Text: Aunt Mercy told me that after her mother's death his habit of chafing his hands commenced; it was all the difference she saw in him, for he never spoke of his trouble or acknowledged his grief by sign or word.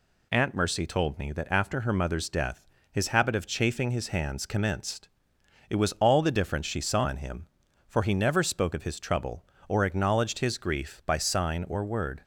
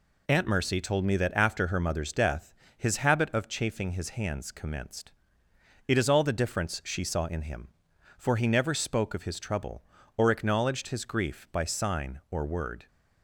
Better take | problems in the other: first | pauses between "death" and "his"; slight; at 2.5 s; 0.25 s long; slight in the first // says "is" for "was"; at 5.9 s

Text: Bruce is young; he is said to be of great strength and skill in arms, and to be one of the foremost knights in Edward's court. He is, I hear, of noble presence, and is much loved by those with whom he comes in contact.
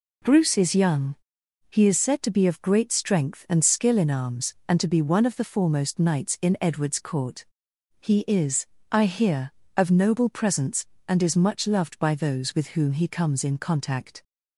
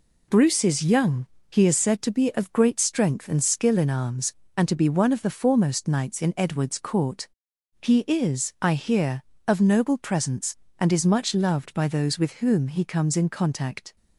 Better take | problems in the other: neither | none

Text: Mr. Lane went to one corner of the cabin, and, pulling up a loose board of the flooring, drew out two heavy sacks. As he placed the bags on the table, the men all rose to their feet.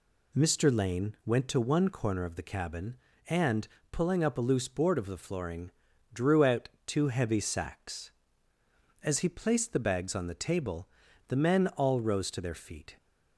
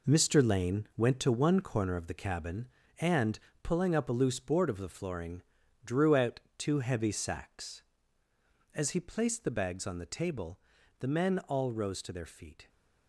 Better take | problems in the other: first | gets quieter; strong; throughout; 9 dB // pauses between "out" and "two"; slight; at 6.3 s; 0.18 s long; slight in the first

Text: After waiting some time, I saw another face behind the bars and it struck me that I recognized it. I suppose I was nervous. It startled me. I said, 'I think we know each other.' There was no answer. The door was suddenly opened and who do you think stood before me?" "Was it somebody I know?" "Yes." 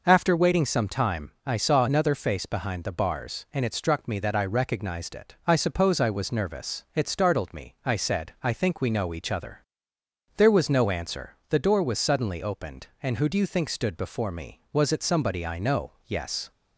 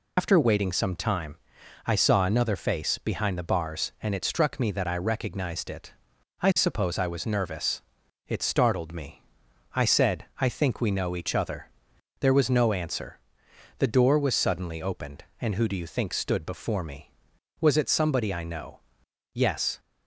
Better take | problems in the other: first | loses the start of "After"; at 0.1 s; 85 ms

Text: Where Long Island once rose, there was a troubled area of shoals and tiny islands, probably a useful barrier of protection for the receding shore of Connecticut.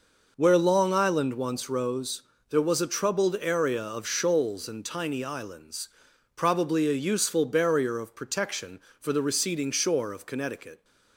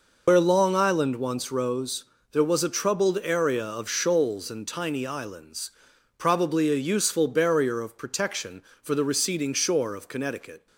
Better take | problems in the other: first | loses the start of "Where"; at 0.2 s; 95 ms

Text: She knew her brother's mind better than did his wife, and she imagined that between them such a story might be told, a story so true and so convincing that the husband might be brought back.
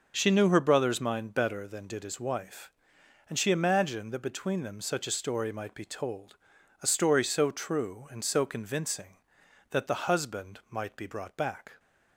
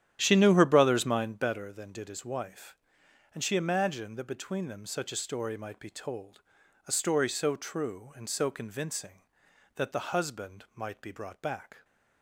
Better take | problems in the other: first | starts louder than the rest; strong; until 1.5 s; 10.5 dB

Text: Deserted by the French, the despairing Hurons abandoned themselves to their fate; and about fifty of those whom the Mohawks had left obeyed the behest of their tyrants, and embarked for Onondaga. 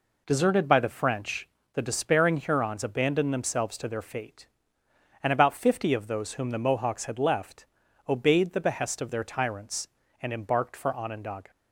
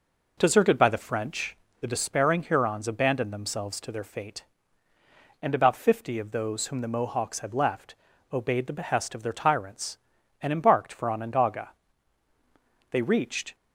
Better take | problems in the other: first | pauses between "left" and "obeyed"; slight; at 7.9 s; 0.36 s long; also in the first // goes on to say "They reached"; noticeable; from 12.9 s on; 0.64 s long

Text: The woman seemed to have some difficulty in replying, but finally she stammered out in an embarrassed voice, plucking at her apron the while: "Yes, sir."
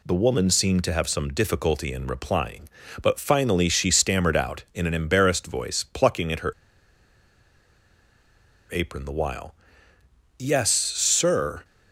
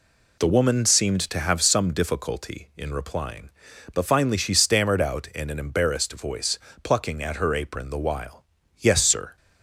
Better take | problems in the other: second | pauses between "her" and "apron"; strong; at 6.5 s; 2.1 s long

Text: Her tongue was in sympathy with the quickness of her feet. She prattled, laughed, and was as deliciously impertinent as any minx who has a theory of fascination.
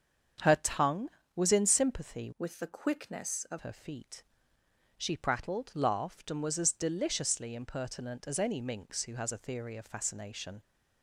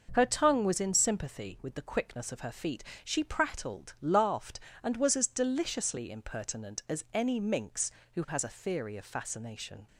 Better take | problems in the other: second | starts louder than the rest; strong; until 1.6 s; 7.5 dB // changes voice from "with" to "of"; from 2.3 to 3.5 s; 1.2 s long

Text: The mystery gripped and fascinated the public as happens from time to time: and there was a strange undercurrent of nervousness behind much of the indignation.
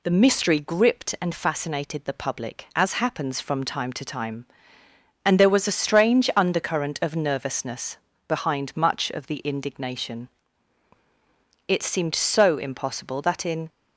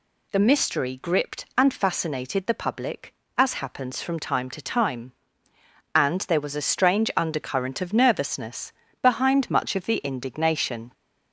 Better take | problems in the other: second | pauses between "nervousness" and "behind"; slight; at 7.9 s; 0.28 s long; slight in the second // goes on to say "It seemed so impossible that in"; strong; from 11.6 s on; 2.0 s long

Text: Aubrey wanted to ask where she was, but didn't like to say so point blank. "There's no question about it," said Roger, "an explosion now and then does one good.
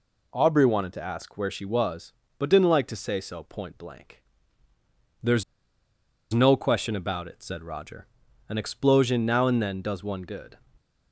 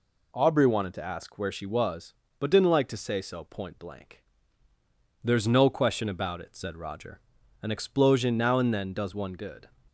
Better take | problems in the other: second | pauses between "There's" and "no"; noticeable; at 5.4 s; 0.90 s long

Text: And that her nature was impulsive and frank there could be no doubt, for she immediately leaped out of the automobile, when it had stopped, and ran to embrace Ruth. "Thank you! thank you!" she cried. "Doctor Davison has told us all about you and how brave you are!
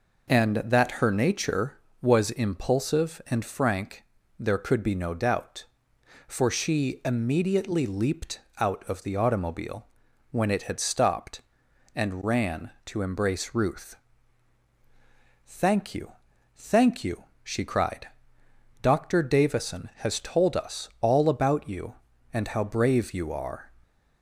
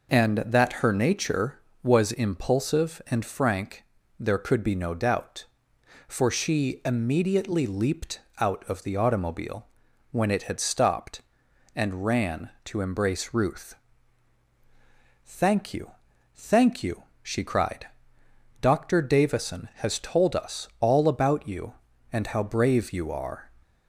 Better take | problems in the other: neither | pauses between "frank" and "there"; slight; the same in both // pauses between "leaped" and "out"; slight; the same in both

